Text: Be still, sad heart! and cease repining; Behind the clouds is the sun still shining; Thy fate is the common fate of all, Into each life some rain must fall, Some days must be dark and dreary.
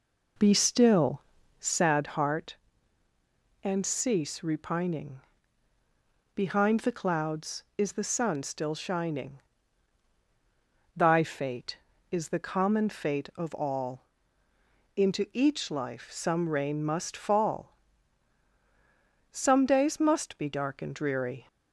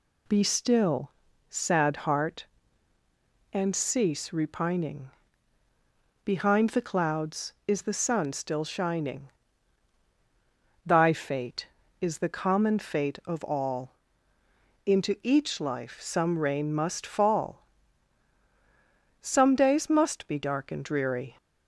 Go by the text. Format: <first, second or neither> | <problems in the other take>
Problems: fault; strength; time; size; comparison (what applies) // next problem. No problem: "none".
second | starts louder than the rest; noticeable; until 1.9 s; 4 dB